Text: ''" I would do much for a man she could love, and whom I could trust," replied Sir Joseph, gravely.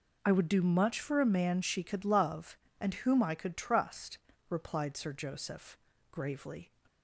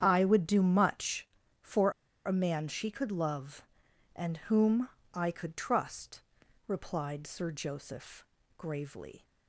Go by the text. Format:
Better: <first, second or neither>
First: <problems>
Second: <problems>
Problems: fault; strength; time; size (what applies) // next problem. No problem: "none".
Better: first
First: none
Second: starts louder than the rest; strong; until 1.0 s; 8.5 dB // pauses between "for" and "a"; slight; at 1.9 s; 0.34 s long // pauses between "whom" and "I"; slight; at 4.8 s; 0.26 s long